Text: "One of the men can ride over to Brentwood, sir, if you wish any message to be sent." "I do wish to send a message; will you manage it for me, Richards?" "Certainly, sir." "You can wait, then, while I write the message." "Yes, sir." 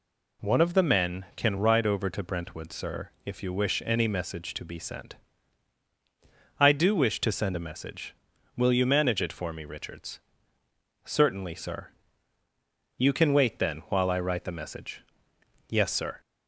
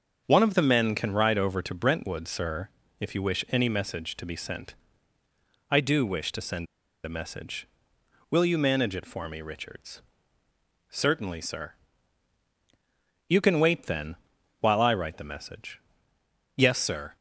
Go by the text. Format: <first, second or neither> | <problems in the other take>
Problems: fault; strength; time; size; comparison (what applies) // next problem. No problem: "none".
first | starts louder than the rest; until 1.2 s; 6.5 dB // pauses between "send" and "a"; at 6.6 s; 0.38 s long